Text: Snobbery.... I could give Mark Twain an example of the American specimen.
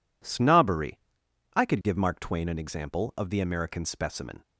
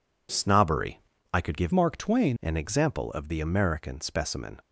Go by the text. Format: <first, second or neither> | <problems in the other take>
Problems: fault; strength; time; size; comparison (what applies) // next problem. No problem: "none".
first | changes voice from "Mark" to "Twain"; from 1.7 to 2.3 s; 0.6 s long